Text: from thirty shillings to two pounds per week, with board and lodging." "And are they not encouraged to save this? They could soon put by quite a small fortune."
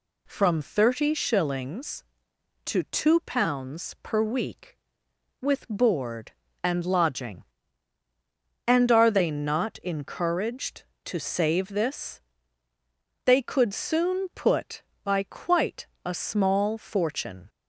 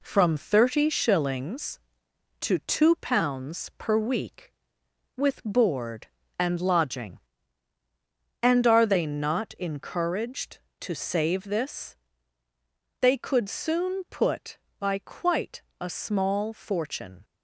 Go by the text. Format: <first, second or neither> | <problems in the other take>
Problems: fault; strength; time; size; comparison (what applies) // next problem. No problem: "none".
first | gets quieter; noticeable; throughout; 4 dB // pauses between "quite" and "a"; slight; at 15.6 s; 0.18 s long; slight in the first